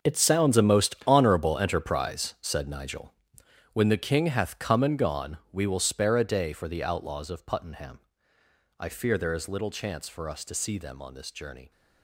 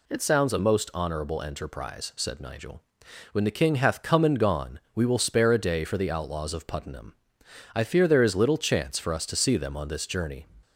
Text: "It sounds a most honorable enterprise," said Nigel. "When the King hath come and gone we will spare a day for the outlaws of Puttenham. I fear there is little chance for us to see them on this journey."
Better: second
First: gets quieter; strong; throughout; 13 dB // pauses between "gone" and "we"; slight; at 5.3 s; 0.16 s long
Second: none

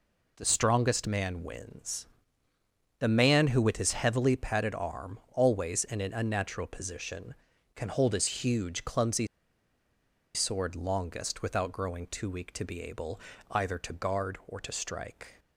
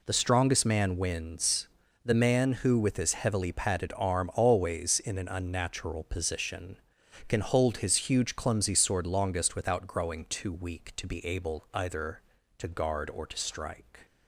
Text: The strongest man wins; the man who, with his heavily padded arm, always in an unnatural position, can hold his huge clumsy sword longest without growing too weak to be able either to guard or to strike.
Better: second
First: pauses between "clumsy" and "sword"; at 9.2 s; 1.0 s long // pauses between "able" and "either"; slight; at 13.1 s; 0.30 s long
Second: none

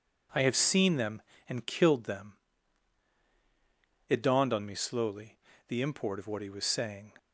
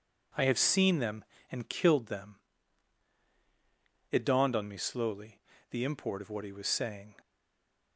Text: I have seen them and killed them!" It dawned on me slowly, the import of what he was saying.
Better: first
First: none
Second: stays silent after the last word; slight; from 7.1 s on; 0.8 s long

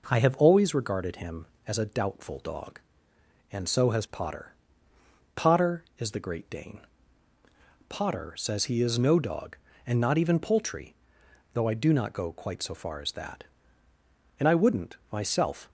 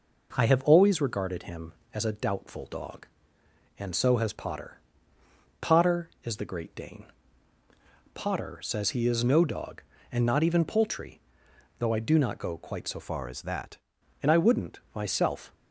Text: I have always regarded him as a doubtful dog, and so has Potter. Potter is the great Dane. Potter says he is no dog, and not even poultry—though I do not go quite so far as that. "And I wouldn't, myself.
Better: first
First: none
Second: changes voice from "far" to "that"; from 13.0 to 13.7 s; 0.7 s long

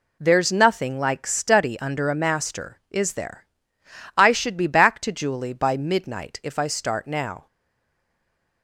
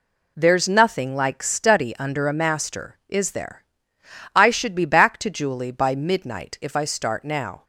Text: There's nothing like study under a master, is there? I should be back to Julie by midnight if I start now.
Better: second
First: stays silent after the last word; noticeable; from 7.4 s on; 1.2 s long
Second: none

